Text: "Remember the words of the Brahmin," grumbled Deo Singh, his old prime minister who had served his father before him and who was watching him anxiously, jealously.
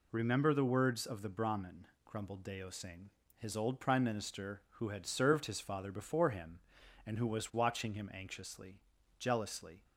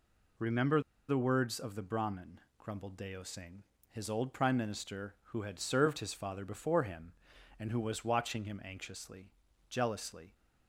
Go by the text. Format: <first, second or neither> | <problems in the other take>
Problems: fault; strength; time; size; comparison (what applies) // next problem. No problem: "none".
first | pauses between "Remember" and "the"; slight; at 0.8 s; 0.26 s long